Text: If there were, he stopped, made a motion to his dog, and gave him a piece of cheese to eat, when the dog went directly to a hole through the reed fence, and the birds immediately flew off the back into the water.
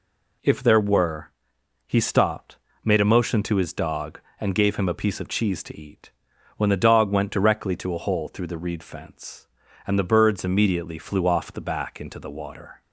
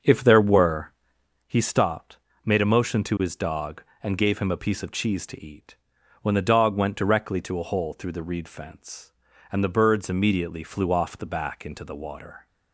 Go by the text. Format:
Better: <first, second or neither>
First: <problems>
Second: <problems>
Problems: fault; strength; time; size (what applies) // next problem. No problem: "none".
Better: first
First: none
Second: starts louder than the rest; until 1.5 s; 6.5 dB